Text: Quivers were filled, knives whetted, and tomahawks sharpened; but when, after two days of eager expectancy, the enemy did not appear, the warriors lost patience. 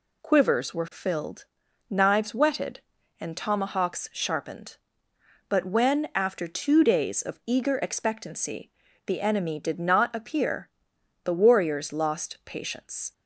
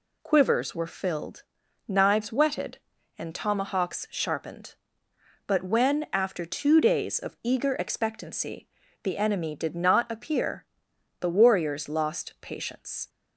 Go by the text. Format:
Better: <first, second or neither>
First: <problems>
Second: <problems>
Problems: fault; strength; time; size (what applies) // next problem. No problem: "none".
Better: neither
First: none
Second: none